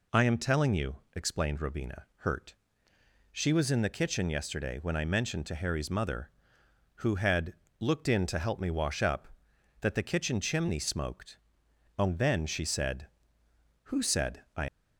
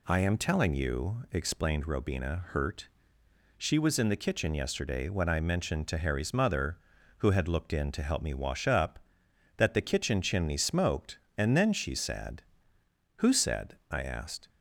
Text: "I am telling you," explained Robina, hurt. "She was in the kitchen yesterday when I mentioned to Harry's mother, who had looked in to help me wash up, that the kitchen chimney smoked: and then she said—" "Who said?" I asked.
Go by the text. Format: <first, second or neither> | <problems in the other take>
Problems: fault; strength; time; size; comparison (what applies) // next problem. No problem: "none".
second | pauses between "had" and "looked"; slight; at 7.5 s; 0.26 s long // stops before "asked"; at 14.6 s